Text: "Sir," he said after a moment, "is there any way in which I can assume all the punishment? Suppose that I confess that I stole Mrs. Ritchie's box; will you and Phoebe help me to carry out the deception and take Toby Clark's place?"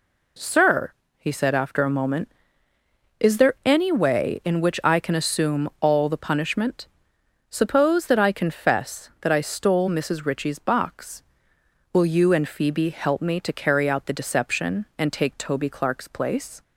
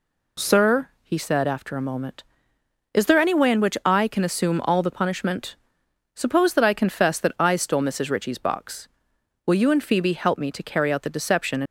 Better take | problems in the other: first | stops before "and take Toby Clark's place"; at 11.6 s

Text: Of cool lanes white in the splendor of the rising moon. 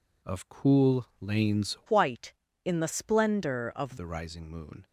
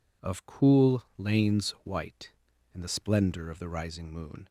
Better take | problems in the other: second | pauses between "cool" and "lanes"; slight; at 1.0 s; 0.16 s long; slight in the second // changes voice from "white" to "of"; from 1.8 to 3.9 s; 2.1 s long

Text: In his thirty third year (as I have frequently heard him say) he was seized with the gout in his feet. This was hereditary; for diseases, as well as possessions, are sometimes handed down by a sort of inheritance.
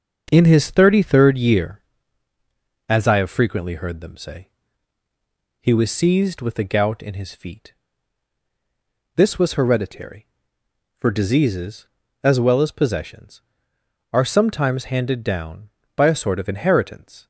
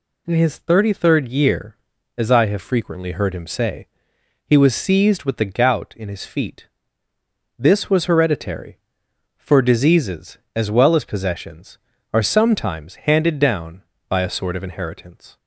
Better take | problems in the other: second | starts louder than the rest; until 1.3 s; 6.5 dB // says "them" for "him"; at 3.9 s

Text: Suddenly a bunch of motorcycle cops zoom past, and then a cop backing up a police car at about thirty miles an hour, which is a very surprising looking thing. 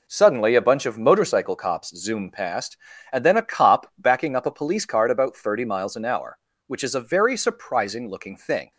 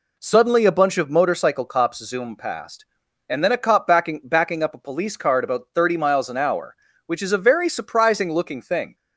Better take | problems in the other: first | says "backing" twice; at 4.2 s

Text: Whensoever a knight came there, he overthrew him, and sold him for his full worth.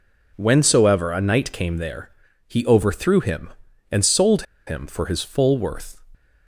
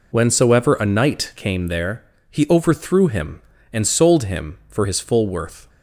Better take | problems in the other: second | pauses between "sold" and "him"; slight; at 4.4 s; 0.24 s long

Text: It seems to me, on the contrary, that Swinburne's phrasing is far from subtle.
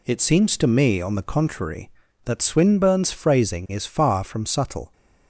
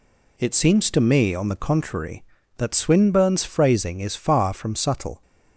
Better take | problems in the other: neither | none

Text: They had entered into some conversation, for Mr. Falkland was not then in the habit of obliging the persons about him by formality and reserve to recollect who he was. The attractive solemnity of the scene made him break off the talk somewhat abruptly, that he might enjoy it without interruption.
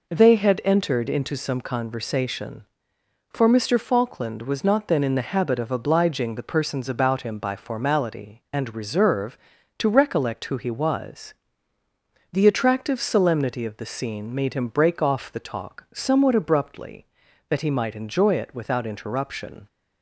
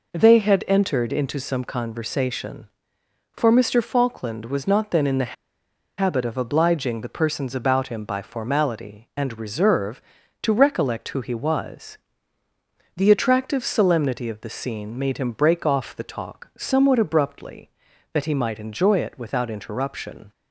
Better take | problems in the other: first | pauses between "the" and "habit"; noticeable; at 5.3 s; 0.65 s long

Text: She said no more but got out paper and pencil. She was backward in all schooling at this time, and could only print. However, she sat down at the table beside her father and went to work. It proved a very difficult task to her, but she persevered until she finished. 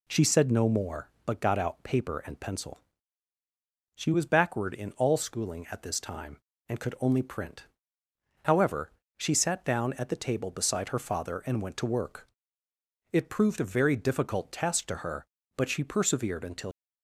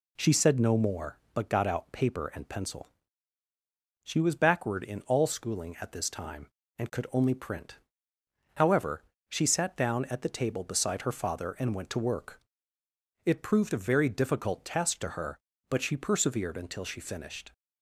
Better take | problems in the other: second | stops before "she finished"; at 16.7 s

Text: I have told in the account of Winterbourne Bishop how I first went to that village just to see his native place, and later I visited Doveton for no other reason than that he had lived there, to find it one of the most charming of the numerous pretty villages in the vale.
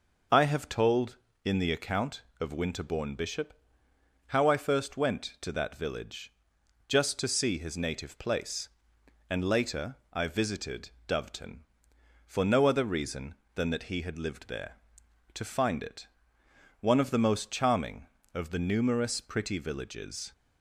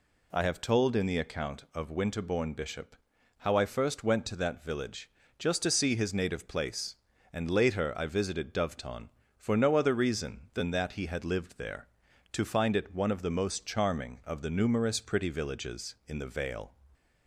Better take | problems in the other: second | pauses between "Bishop" and "how"; noticeable; at 3.5 s; 0.74 s long; also in the second // pauses between "village" and "just"; noticeable; at 6.3 s; 0.54 s long; slight in the second // pauses between "later" and "I"; slight; at 9.9 s; 0.16 s long // pauses between "visited" and "Doveton"; slight; at 10.9 s; 0.18 s long // pauses between "it" and "one"; noticeable; at 16.0 s; 0.74 s long // stops before "in the vale"; at 20.3 s

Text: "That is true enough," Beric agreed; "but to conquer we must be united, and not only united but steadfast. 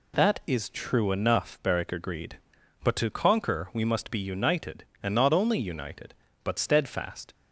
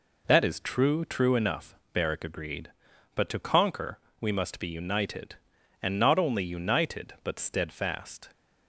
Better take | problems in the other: first | says "true" twice; at 1.0 s // pauses between "conquer" and "we"; slight; at 3.9 s; 0.20 s long

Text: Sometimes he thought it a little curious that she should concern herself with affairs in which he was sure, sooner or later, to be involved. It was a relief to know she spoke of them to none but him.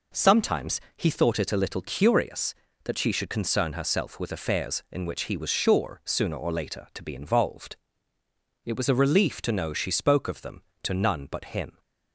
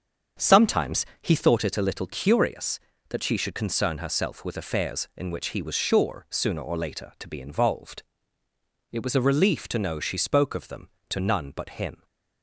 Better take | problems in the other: first | starts louder than the rest; strong; until 1.6 s; 7 dB // pauses between "Sometimes" and "he"; slight; at 1.0 s; 0.16 s long; slight in the first

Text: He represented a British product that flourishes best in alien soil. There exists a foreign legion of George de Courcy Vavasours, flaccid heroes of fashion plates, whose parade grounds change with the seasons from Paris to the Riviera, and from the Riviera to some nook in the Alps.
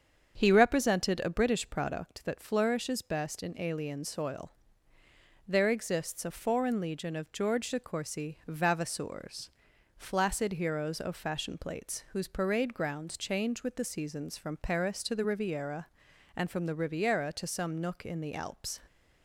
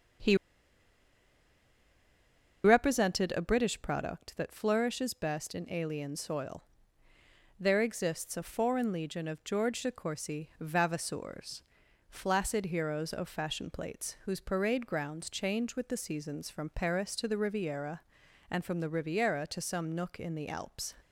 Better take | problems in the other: first | starts louder than the rest; strong; until 3.5 s; 7 dB; strong in the first // pauses between "He" and "represented"; strong; at 0.3 s; 2.2 s long

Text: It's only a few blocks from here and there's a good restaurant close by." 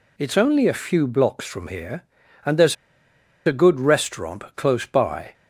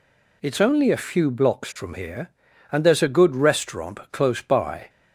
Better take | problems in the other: second | pauses between "there's" and "a"; noticeable; at 2.7 s; 0.71 s long

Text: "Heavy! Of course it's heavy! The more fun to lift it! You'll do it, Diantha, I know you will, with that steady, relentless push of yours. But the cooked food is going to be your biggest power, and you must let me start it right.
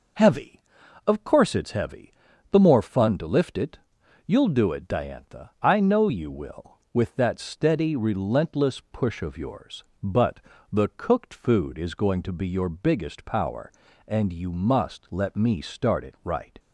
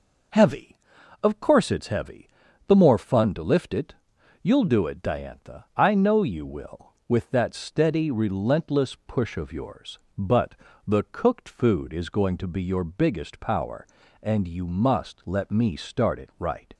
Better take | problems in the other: neither | pauses between "But" and "the"; slight; the same in both

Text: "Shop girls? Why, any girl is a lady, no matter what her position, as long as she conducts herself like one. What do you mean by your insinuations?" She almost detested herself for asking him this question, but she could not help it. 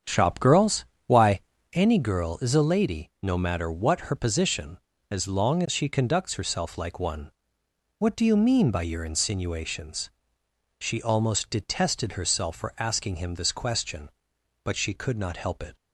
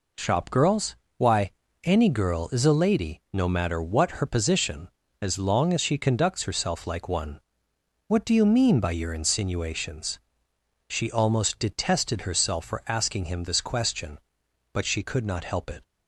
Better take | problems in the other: second | starts louder than the rest; strong; until 1.8 s; 8 dB

